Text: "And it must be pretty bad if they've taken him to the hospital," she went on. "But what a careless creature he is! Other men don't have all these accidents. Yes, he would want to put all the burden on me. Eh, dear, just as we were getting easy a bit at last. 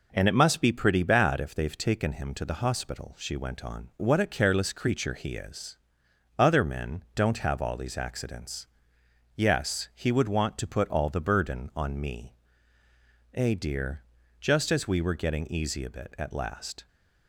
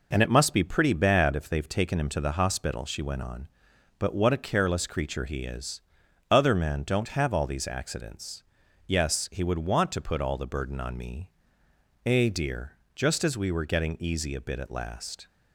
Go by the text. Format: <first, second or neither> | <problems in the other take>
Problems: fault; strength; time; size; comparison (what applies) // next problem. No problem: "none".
second | skips "But"; at 3.9 s